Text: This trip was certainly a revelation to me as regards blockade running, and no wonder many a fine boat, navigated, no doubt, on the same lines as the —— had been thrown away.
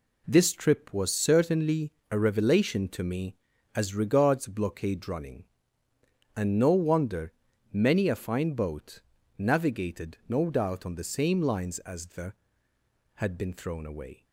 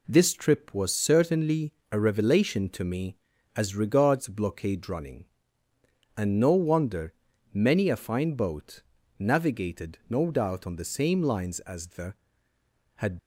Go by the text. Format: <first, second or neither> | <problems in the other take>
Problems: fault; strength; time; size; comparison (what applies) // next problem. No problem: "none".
first | pauses between "certainly" and "a"; slight; at 1.7 s; 0.18 s long; slight in the first // pauses between "wonder" and "many"; at 7.1 s; 0.40 s long; also in the first // stops before "been thrown away"; at 13.1 s